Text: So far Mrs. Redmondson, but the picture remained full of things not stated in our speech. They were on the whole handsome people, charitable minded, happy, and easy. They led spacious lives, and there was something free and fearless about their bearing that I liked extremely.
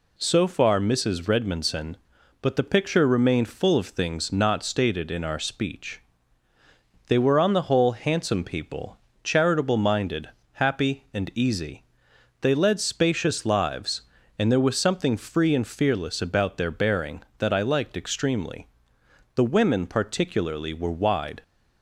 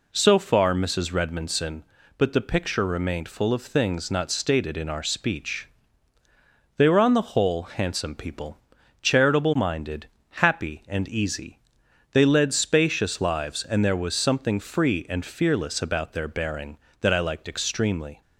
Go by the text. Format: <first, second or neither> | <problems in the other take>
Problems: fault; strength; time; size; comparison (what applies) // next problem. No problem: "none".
second | goes on to say "The women particularly were wide"; strong; from 19.3 s on; 2.0 s long